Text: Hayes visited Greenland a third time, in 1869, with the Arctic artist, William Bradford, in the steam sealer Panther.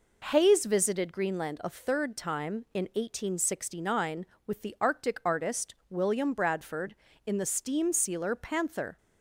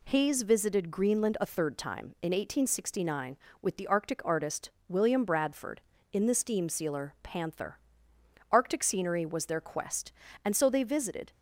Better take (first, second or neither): first